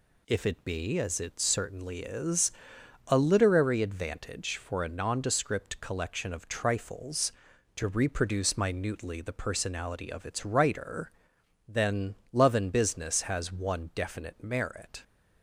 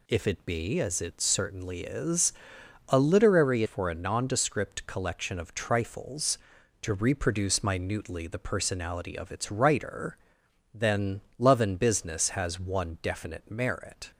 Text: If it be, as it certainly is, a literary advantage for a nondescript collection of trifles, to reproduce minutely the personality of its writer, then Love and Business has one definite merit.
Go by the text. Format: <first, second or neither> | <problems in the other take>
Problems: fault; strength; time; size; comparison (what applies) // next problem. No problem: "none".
first | skips "advantage"; at 3.6 s // pauses between "then" and "Love"; slight; at 11.2 s; 0.18 s long; slight in the first